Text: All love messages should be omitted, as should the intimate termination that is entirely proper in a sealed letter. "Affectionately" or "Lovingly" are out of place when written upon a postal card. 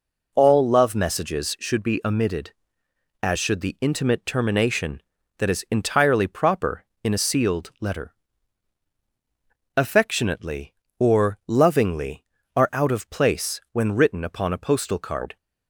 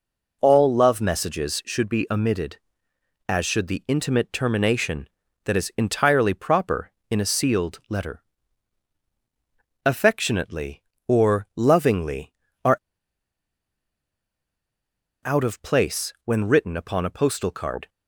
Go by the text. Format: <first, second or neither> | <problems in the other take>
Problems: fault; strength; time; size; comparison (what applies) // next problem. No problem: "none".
first | pauses between "are" and "out"; strong; at 12.7 s; 2.4 s long